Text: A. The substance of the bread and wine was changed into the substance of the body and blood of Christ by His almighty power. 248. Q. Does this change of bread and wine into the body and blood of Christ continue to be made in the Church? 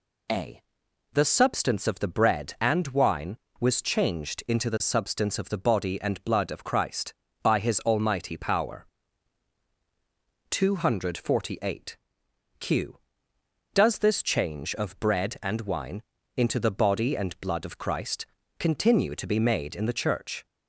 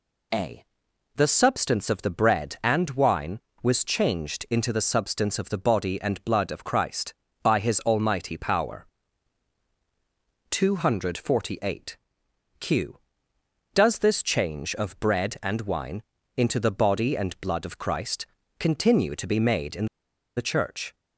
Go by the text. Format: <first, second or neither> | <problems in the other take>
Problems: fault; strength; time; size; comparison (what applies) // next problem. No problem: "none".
first | pauses between "wine" and "into"; slight; at 16.0 s; 0.34 s long; slight in the first // pauses between "Christ" and "continue"; slight; at 18.2 s; 0.32 s long; slight in the first // pauses between "in" and "the"; noticeable; at 19.8 s; 0.51 s long